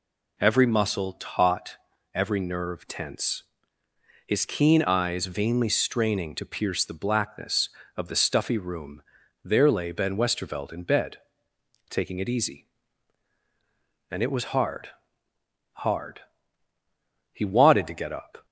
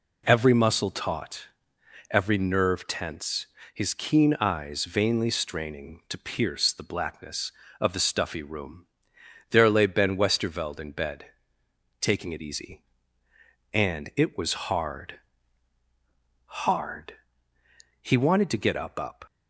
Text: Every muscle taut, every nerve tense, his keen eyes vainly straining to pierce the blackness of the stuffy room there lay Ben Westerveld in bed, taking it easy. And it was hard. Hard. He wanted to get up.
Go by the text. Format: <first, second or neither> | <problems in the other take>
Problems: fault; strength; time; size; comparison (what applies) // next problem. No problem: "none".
first | pauses between "room" and "there"; noticeable; at 8.8 s; 0.64 s long; also in the first // says "up" twice; at 18.9 s